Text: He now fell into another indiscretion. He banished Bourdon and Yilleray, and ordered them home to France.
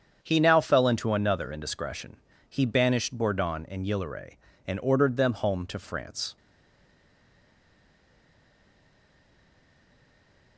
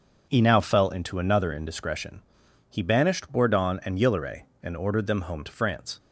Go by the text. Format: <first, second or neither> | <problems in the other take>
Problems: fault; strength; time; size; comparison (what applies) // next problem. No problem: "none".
second | starts louder than the rest; strong; until 1.2 s; 7.5 dB; also in the second // stays silent after the last word; strong; from 6.3 s on; 4.2 s long